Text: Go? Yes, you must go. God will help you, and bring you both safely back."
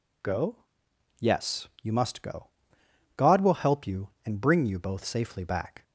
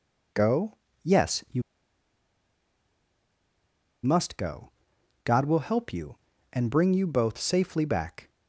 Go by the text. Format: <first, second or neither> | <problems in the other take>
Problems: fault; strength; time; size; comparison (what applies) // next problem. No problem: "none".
first | pauses between "you" and "must"; strong; at 1.6 s; 2.4 s long